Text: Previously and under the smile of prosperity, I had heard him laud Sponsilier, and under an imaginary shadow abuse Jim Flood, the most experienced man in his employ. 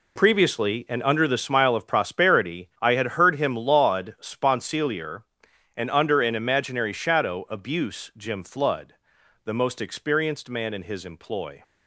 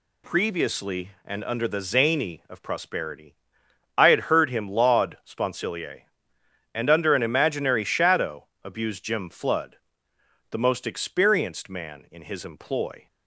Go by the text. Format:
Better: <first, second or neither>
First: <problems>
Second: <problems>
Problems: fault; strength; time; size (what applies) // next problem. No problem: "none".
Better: first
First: none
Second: says "zany" for "smile"; at 1.8 s // pauses between "shadow" and "abuse"; slight; at 8.4 s; 0.16 s long